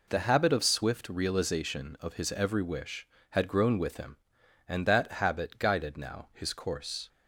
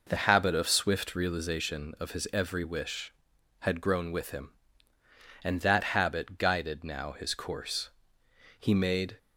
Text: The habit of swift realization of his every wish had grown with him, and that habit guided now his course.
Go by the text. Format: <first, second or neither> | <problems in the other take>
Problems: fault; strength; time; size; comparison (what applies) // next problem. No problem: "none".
first | goes on to say "He made"; from 8.6 s on; 0.56 s long